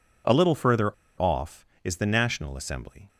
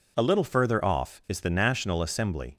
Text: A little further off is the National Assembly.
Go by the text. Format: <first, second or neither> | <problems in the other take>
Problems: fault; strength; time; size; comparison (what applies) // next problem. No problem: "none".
second | pauses between "further" and "off"; slight; at 0.9 s; 0.27 s long